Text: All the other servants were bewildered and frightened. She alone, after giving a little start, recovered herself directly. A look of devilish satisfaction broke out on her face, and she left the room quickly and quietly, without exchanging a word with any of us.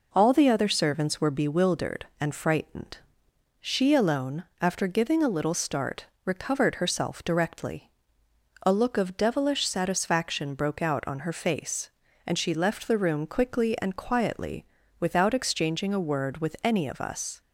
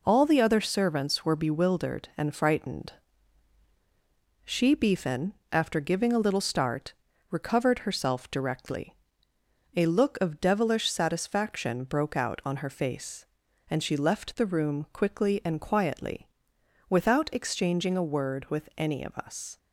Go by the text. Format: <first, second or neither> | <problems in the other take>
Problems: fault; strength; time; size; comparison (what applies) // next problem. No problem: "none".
first | says "beefin" for "alone"; at 4.7 s